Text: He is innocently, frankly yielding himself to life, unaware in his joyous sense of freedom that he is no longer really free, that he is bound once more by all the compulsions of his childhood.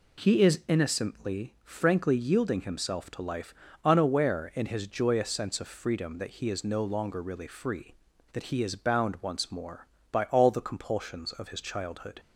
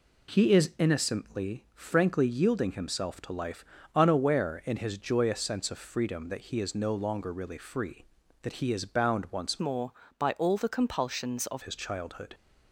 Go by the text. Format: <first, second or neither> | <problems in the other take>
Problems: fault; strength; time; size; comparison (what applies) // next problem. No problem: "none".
first | changes voice from "more" to "of"; from 9.5 to 11.6 s; 2.1 s long